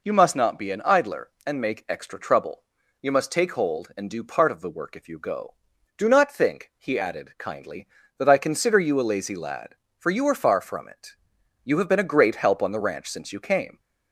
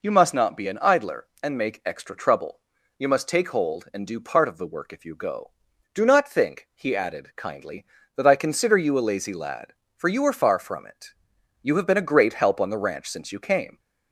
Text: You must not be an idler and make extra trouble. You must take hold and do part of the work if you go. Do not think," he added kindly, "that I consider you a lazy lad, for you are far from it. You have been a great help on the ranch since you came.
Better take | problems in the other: neither | none

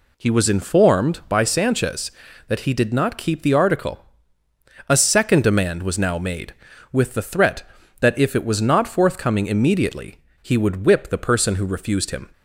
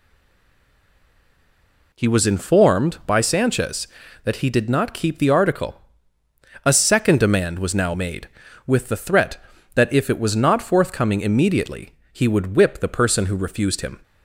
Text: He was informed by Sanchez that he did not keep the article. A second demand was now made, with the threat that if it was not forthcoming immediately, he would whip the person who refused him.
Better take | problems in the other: first | stays silent before the first word; noticeable; until 1.9 s; 1.9 s long

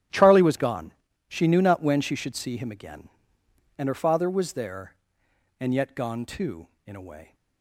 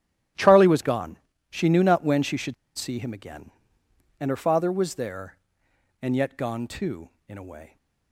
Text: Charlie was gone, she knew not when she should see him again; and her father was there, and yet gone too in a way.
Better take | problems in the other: first | starts louder than the rest; strong; until 1.6 s; 12.5 dB; strong in the first // pauses between "should" and "see"; slight; at 2.5 s; 0.23 s long

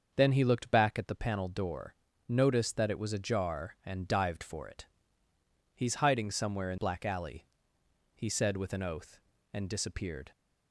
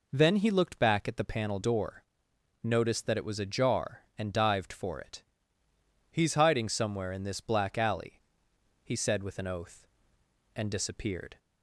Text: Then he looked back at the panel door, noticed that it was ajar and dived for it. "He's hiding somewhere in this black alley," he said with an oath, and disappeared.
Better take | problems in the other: second | starts louder than the rest; until 1.1 s; 6.5 dB // skips "this"; at 6.7 s

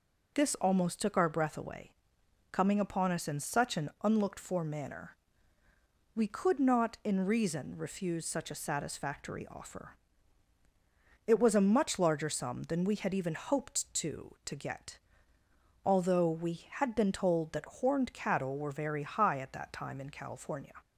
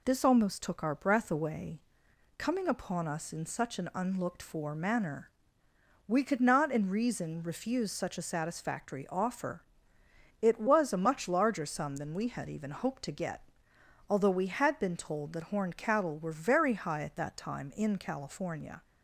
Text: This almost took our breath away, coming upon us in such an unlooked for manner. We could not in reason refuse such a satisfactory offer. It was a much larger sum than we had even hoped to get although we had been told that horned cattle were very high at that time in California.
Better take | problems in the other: second | says "to" twice; at 14.4 s // pauses between "get" and "although"; noticeable; at 14.9 s; 0.86 s long; noticeable in the second

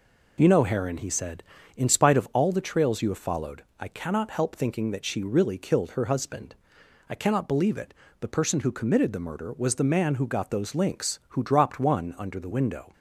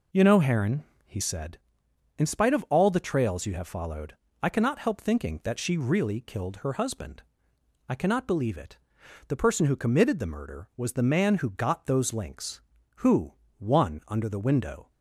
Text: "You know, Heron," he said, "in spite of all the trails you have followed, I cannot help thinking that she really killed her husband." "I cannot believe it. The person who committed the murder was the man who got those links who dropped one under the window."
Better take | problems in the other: first | skips "dropped"; at 13.4 s

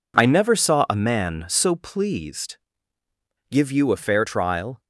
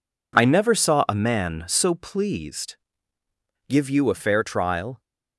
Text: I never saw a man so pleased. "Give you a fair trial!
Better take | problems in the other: neither | none

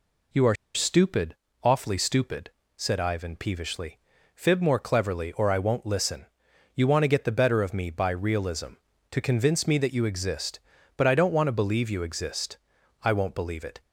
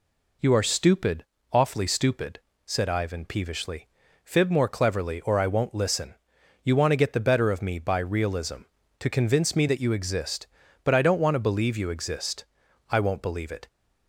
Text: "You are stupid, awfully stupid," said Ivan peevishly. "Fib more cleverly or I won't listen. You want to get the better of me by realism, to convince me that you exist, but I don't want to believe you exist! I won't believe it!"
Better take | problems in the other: second | pauses between "are" and "stupid"; slight; at 0.5 s; 0.19 s long

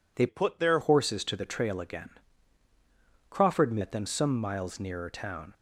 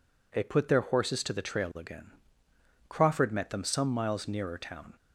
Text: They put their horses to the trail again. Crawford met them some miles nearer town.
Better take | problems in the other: second | changes voice from "put" to "their"; from 0.2 to 0.7 s; 0.5 s long

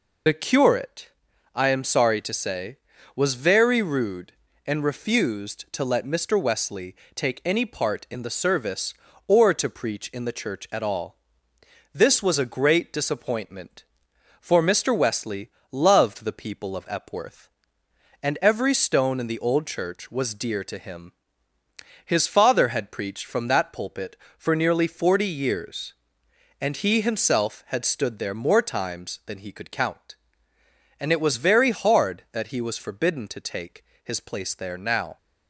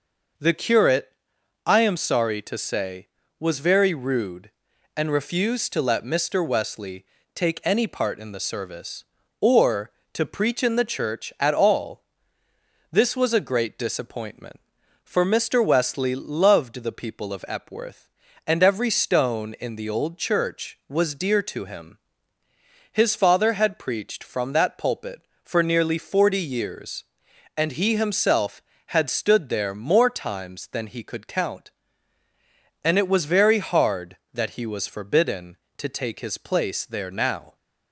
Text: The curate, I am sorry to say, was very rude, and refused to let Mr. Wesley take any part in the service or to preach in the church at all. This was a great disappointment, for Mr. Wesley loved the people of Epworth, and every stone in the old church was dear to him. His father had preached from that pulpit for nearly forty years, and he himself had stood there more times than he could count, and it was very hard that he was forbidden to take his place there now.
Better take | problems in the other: second | loses the start of "The"; at 0.2 s; 40 ms // pauses between "Wesley" and "take"; slight; at 6.9 s; 0.20 s long; slight in the second // pauses between "Wesley" and "loved"; slight; at 15.4 s; 0.22 s long // pauses between "take" and "his"; slight; at 33.8 s; 0.20 s long

